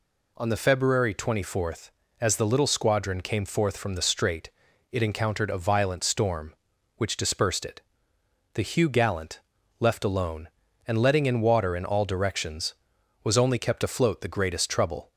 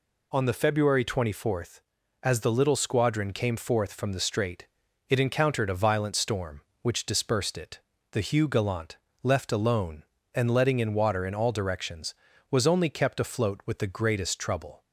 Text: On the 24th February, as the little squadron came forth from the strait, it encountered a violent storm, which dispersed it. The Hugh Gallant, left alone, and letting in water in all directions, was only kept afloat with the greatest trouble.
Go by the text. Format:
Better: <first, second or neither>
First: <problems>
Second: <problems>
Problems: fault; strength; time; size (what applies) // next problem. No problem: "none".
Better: second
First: skips "with"; at 14.2 s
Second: none